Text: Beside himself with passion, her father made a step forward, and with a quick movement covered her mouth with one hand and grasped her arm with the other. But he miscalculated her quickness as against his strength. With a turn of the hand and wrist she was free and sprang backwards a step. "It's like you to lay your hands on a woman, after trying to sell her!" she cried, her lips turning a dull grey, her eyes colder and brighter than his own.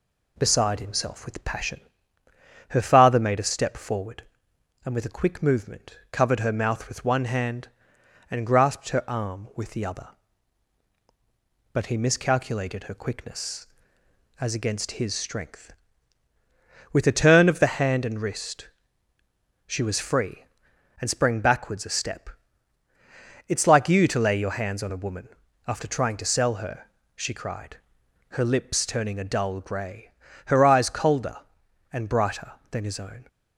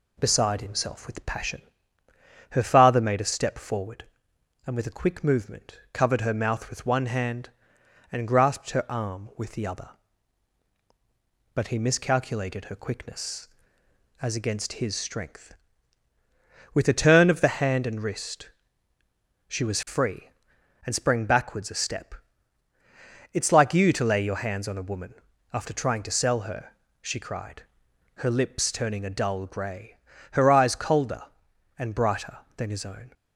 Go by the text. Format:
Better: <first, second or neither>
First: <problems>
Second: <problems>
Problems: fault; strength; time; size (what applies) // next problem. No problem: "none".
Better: neither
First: pauses between "wrist" and "she"; noticeable; at 18.6 s; 0.96 s long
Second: pauses between "wrist" and "she"; noticeable; at 18.5 s; 0.96 s long